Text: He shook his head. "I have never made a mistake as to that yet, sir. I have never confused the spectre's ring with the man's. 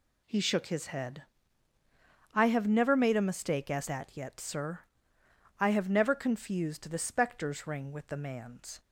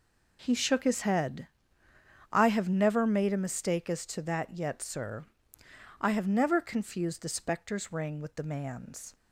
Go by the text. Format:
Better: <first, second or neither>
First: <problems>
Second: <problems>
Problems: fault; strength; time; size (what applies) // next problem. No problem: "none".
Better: second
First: skips "to"; at 3.8 s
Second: none